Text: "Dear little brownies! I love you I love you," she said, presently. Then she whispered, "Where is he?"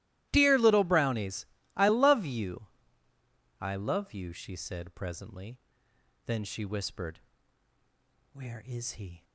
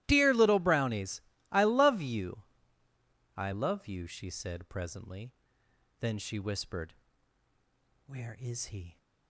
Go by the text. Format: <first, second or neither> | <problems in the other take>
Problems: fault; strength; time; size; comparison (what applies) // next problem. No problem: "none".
neither | starts louder than the rest; strong; the same in both // pauses between "you" and "I"; noticeable; the same in both